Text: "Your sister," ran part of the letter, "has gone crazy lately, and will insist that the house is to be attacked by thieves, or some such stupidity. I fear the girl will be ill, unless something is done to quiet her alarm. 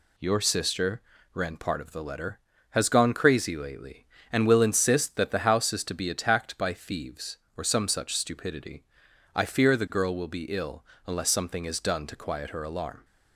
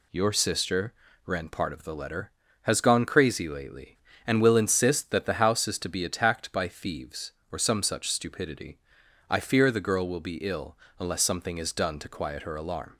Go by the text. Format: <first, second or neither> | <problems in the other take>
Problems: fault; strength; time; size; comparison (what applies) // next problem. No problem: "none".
neither | none